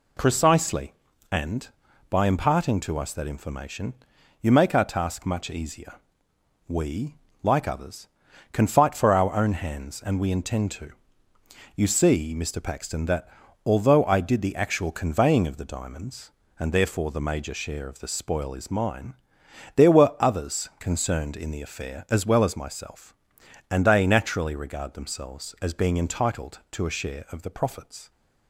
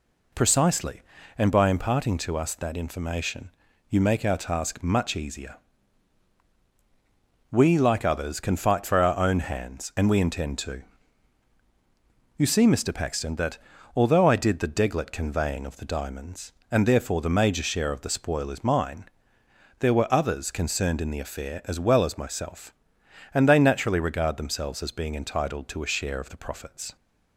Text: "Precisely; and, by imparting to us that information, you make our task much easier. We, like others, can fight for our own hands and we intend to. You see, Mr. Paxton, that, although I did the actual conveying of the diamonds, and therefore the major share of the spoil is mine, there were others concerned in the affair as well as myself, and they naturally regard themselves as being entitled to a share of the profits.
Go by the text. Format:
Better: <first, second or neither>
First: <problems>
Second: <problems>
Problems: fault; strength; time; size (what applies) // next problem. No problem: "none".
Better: first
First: none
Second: says "deglet" for "actual"; at 14.6 s